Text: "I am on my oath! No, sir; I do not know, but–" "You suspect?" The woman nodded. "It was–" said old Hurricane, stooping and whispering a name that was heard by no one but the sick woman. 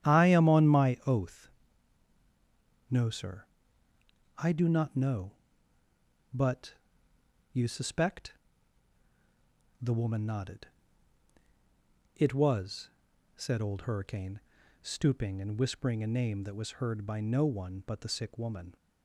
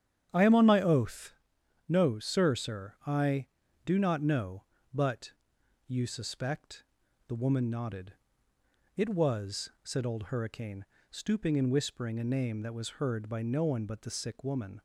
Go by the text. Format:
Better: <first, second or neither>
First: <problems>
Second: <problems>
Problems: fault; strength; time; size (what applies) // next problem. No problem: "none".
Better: first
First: starts louder than the rest; strong; until 1.1 s; 10.5 dB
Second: starts louder than the rest; strong; until 1.3 s; 9.5 dB // says "sir" twice; at 2.5 s